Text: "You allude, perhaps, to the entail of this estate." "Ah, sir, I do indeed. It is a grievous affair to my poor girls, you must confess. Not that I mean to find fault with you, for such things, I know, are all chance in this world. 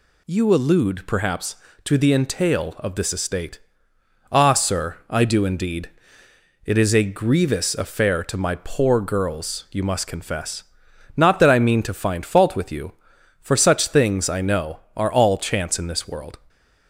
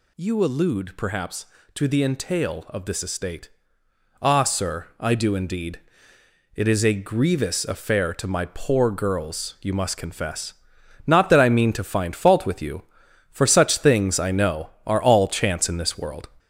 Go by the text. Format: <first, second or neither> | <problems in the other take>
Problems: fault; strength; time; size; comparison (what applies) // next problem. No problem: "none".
first | gets louder; noticeable; throughout; 4.5 dB